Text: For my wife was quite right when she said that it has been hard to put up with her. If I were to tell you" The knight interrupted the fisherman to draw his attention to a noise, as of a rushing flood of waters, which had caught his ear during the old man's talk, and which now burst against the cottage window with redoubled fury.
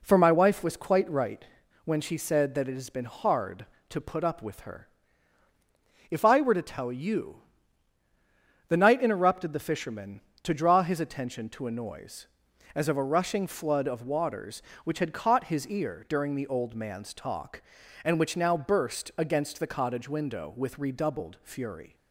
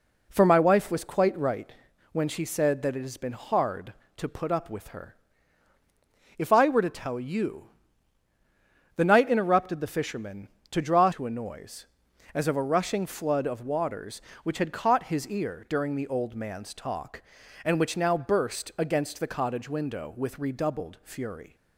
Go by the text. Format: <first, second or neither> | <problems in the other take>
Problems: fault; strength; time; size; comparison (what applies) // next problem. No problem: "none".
first | pauses between "right" and "when"; at 1.7 s; 0.40 s long; also in the first // pauses between "you" and "The"; strong; at 7.6 s; 1.3 s long; strong in the first // skips "his attention"; at 11.1 s